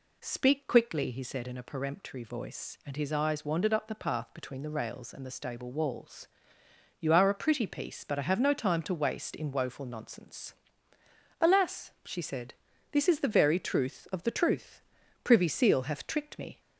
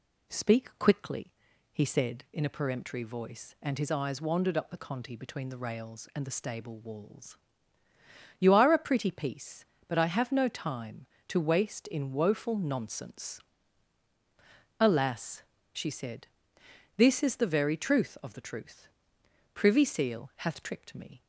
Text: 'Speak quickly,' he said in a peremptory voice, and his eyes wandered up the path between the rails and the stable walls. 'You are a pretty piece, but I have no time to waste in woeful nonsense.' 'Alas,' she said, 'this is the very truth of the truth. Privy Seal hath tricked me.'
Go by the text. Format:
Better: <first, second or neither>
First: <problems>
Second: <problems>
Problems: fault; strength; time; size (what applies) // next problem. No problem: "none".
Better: first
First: none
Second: says "conti" for "path"; at 4.7 s